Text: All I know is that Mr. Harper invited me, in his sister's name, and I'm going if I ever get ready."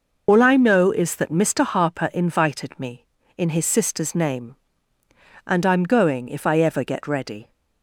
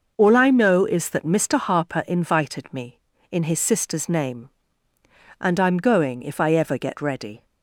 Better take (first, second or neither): second